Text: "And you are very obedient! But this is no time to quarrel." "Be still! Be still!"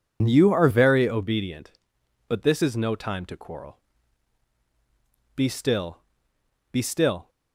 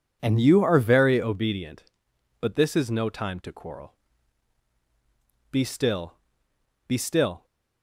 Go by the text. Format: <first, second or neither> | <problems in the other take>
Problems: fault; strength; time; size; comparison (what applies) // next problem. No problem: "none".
second | loses the start of "And"; at 0.2 s; 95 ms